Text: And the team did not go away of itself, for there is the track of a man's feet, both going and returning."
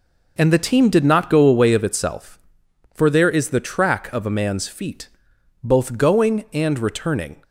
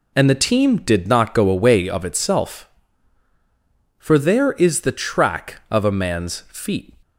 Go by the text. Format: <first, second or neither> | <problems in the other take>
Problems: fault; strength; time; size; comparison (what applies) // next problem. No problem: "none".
first | stops before "both going and returning"; at 7.0 s